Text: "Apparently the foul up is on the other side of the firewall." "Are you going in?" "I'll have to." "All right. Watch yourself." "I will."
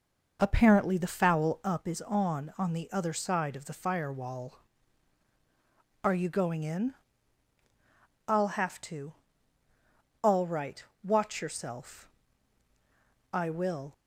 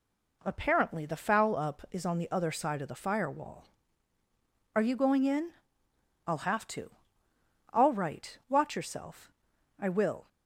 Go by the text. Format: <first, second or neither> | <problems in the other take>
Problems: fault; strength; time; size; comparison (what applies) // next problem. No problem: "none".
second | says "on" twice; at 2.5 s